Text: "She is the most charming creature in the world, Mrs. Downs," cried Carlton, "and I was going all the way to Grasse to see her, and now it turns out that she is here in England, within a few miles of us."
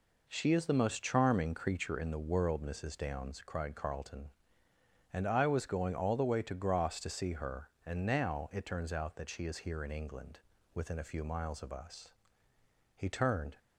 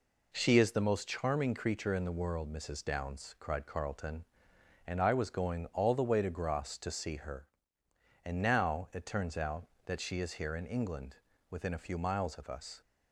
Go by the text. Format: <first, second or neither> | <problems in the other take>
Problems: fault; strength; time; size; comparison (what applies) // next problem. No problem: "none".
second | goes on to say "He turned"; from 12.9 s on; 0.60 s long